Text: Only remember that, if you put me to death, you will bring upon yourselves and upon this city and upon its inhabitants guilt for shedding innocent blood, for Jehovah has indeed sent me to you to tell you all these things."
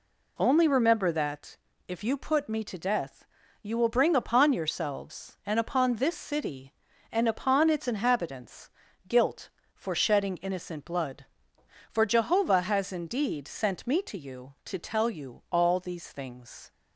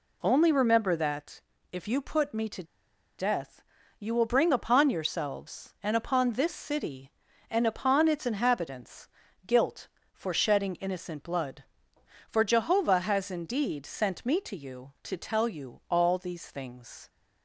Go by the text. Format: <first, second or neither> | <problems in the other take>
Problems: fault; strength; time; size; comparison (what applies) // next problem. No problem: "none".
first | pauses between "to" and "death"; noticeable; at 2.6 s; 0.54 s long // pauses between "inhabitants" and "guilt"; at 9.0 s; 0.38 s long; also in the first